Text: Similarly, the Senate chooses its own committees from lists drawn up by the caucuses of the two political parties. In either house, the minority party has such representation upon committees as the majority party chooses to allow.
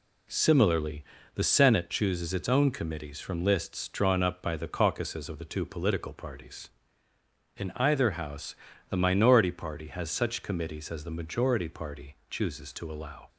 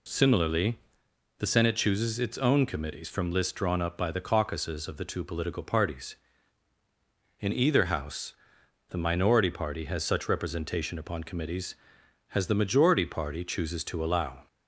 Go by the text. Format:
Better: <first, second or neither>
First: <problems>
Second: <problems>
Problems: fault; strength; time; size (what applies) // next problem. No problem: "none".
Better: second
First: skips "representation upon"; at 10.4 s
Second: none